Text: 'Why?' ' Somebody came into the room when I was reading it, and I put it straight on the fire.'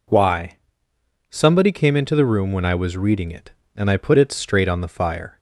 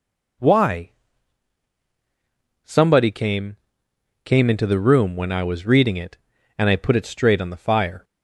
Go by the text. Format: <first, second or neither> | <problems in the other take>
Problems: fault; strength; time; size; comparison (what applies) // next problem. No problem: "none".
first | says "came" twice; at 4.2 s